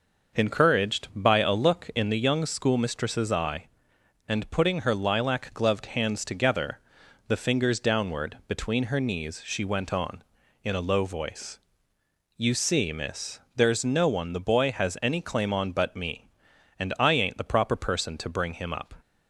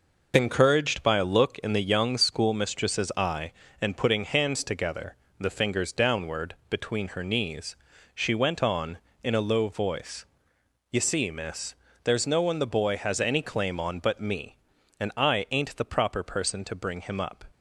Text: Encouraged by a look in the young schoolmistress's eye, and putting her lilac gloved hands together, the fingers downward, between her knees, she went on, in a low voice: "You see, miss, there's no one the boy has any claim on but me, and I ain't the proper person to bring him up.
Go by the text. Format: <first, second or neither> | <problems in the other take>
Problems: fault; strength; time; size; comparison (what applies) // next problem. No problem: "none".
first | skips "her lilac gloved"; at 4.2 s